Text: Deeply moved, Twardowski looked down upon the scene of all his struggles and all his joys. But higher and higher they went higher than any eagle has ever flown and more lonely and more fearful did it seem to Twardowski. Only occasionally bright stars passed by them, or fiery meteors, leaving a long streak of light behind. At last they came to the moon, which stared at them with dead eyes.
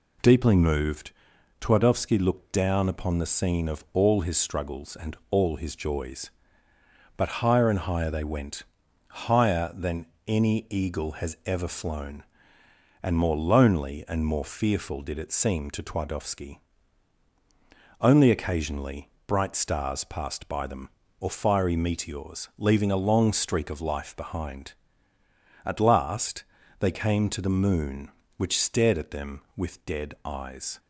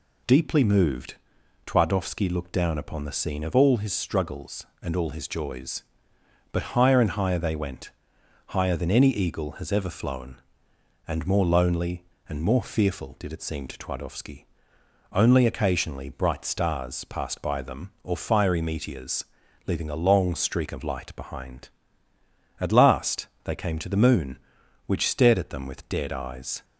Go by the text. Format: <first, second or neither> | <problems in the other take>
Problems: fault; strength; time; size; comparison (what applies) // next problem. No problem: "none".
second | pauses between "went" and "higher"; noticeable; at 8.6 s; 0.48 s long; noticeable in the second // pauses between "than" and "any"; slight; at 10.0 s; 0.20 s long // pauses between "occasionally" and "bright"; slight; at 19.0 s; 0.18 s long // says "life" for "light"; at 23.8 s // pauses between "last" and "they"; slight; at 26.4 s; 0.36 s long; slight in the second